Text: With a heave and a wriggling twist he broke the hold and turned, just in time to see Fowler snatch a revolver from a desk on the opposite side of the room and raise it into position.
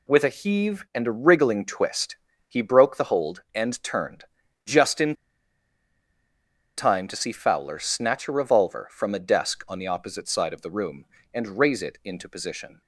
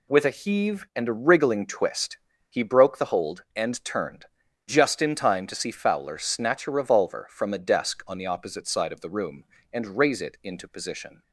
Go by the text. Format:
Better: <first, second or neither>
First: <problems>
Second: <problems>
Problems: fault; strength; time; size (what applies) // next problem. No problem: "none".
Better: second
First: pauses between "twist" and "he"; slight; at 2.1 s; 0.32 s long // pauses between "in" and "time"; strong; at 5.1 s; 1.6 s long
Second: pauses between "twist" and "he"; slight; at 2.1 s; 0.32 s long